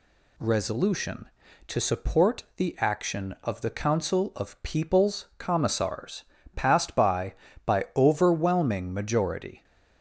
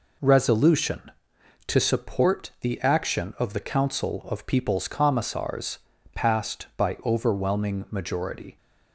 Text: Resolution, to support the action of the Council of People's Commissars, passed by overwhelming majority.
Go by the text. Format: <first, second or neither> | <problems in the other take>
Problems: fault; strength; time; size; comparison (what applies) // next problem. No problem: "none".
second | says "by" twice; at 7.6 s